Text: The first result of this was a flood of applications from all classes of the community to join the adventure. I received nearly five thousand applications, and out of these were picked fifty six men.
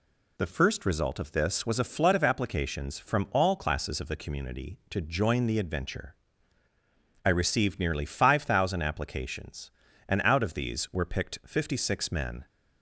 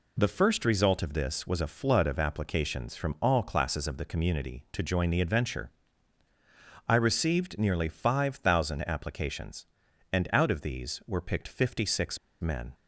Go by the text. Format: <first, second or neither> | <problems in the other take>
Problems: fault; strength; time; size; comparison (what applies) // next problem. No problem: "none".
first | pauses between "six" and "men"; slight; at 12.1 s; 0.23 s long